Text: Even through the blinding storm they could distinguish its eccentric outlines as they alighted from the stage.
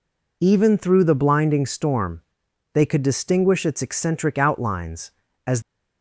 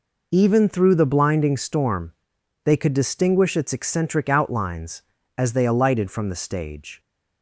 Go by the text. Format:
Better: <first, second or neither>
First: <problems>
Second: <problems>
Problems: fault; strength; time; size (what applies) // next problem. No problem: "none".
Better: second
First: pauses between "storm" and "they"; noticeable; at 2.2 s; 0.52 s long // stops before "they alighted from the stage"; at 5.6 s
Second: pauses between "storm" and "they"; noticeable; at 2.1 s; 0.52 s long